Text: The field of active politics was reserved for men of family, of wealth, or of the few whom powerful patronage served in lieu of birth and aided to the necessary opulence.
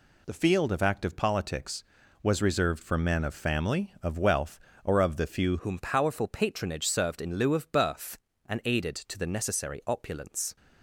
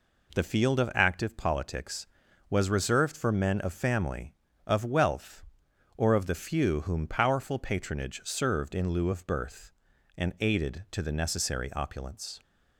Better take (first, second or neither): second